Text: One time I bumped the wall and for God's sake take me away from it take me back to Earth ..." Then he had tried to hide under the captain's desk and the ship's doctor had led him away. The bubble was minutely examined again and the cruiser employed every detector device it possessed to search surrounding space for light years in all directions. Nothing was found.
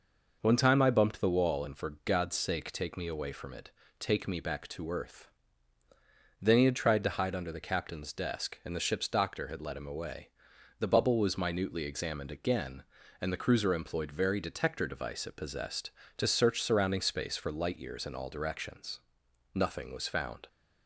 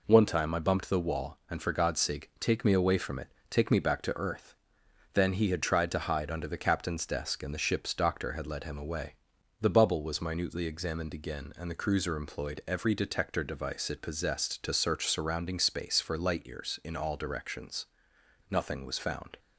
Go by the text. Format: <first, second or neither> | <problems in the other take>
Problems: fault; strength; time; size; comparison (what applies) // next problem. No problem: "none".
second | pauses between "it" and "take"; slight; at 3.7 s; 0.28 s long; slight in the second // says "very" for "every"; at 14.1 s